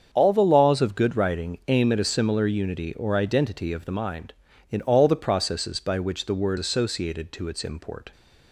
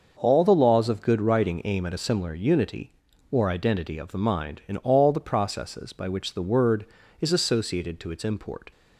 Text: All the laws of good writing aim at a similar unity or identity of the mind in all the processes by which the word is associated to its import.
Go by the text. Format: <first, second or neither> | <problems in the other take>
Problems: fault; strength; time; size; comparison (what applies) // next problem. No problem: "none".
second | starts louder than the rest; strong; until 1.1 s; 7.5 dB; also in the second // skips "is"; at 6.5 s